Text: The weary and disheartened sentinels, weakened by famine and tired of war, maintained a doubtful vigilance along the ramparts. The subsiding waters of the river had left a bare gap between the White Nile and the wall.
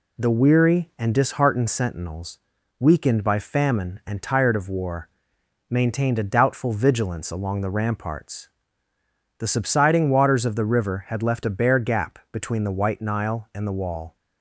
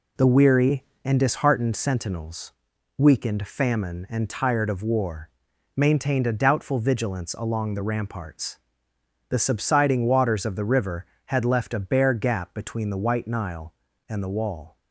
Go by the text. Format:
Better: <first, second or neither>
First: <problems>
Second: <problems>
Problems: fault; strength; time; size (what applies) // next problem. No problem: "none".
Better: first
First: none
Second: skips "by"; at 3.4 s